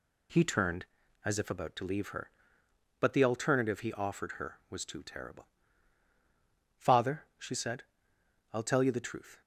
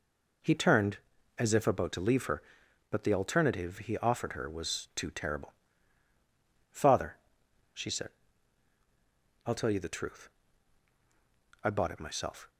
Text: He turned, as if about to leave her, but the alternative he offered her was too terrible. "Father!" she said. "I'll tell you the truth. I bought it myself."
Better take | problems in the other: second | stops before "I bought it myself"; at 9.4 s

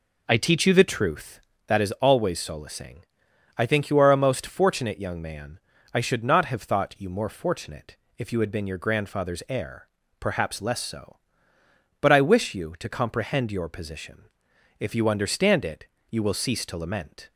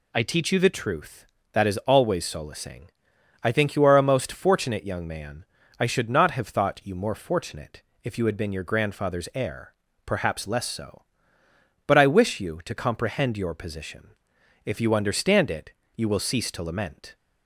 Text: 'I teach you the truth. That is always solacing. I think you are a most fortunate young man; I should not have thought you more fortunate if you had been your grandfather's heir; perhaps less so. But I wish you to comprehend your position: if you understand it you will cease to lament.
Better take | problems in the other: second | starts louder than the rest; noticeable; until 1.6 s; 4.5 dB // pauses between "fortunate" and "if"; slight; at 7.9 s; 0.22 s long; slight in the second // pauses between "it" and "you"; slight; at 15.8 s; 0.24 s long; slight in the second

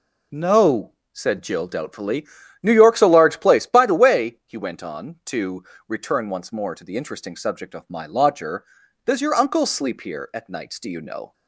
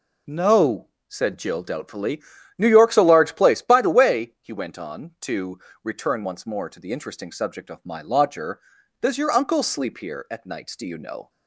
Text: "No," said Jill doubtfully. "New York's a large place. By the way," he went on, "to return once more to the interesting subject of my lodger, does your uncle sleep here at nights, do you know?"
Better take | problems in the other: neither | pauses between "to" and "return"; slight; the same in both

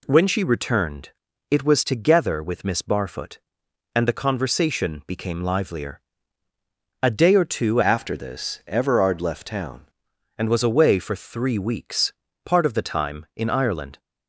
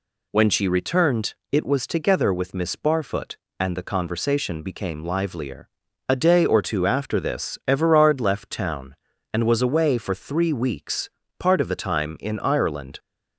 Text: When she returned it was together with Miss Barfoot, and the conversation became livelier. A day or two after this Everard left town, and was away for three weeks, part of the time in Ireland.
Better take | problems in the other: second | pauses between "returned" and "it"; at 1.0 s; 0.40 s long; slight in the second // changes voice from "after" to "town"; from 7.8 to 9.8 s; 2.0 s long

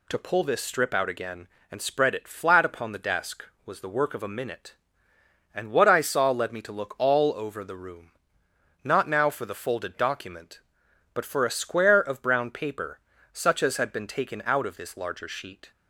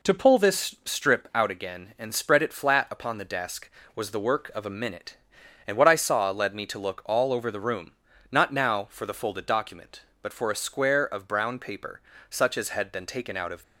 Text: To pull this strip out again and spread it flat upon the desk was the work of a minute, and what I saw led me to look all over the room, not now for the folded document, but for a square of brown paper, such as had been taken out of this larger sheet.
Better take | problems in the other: first | stops before "this larger sheet"; at 13.6 s

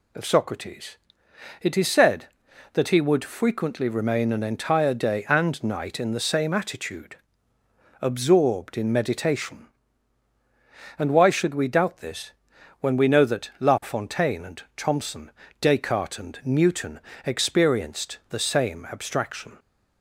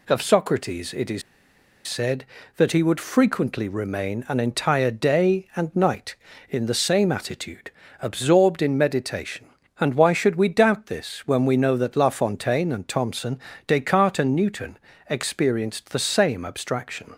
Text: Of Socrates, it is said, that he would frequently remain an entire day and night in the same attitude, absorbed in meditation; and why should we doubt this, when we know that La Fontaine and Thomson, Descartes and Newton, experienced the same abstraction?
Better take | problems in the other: first | pauses between "is" and "said"; noticeable; at 1.2 s; 0.65 s long

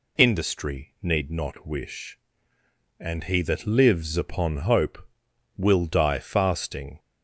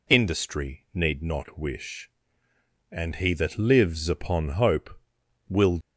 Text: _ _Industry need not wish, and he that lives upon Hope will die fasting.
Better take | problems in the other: first | stops before "die fasting"; at 5.8 s

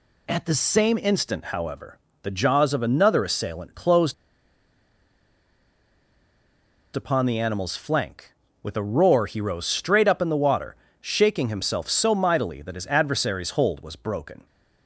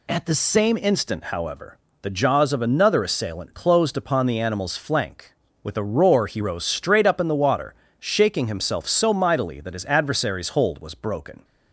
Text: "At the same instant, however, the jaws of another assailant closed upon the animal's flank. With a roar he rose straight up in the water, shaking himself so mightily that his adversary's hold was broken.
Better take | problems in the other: second | pauses between "closed" and "upon"; strong; at 4.1 s; 2.8 s long

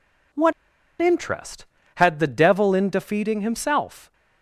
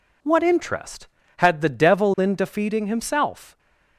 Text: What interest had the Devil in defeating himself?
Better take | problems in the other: second | pauses between "What" and "interest"; noticeable; at 0.5 s; 0.47 s long

